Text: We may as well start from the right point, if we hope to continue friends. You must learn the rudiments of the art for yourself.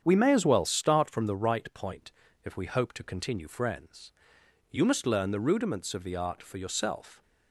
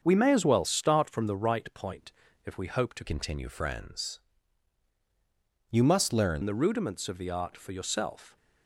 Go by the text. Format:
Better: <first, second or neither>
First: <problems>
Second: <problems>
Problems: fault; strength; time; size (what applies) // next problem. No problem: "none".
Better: first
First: starts louder than the rest; strong; until 1.0 s; 8 dB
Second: starts louder than the rest; until 1.0 s; 7 dB // changes voice from "continue" to "learn"; from 3.0 to 6.4 s; 3.4 s long